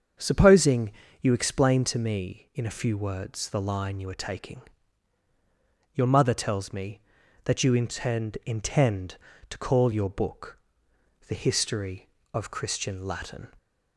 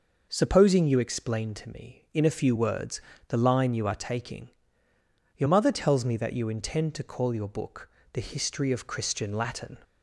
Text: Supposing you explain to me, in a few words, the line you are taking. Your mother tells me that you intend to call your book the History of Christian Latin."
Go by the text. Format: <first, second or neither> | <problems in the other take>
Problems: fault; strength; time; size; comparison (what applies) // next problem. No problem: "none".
second | starts louder than the rest; strong; until 1.5 s; 7 dB // pauses between "Supposing" and "you"; slight; at 0.9 s; 0.30 s long // says "intend" twice; at 8.4 s // pauses between "book" and "the"; noticeable; at 10.5 s; 0.70 s long; slight in the second